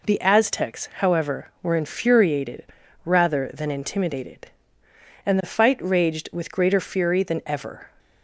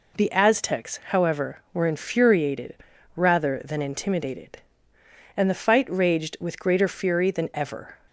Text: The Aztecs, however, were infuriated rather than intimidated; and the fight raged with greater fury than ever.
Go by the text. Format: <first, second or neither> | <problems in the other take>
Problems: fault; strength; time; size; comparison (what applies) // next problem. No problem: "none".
neither | pauses between "infuriated" and "rather"; the same in both